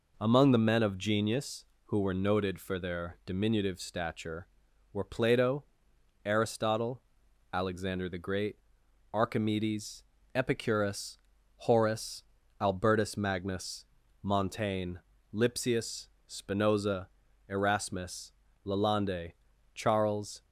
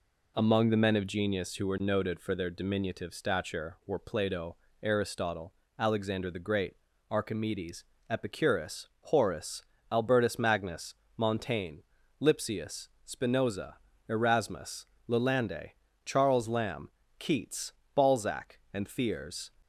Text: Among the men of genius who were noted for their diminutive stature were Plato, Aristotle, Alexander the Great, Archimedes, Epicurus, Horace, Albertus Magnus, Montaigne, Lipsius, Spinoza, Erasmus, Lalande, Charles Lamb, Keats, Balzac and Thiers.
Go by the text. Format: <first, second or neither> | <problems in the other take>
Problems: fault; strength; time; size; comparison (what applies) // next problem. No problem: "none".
second | stops before "Lamb Keats Balzac and Thiers"; at 20.4 s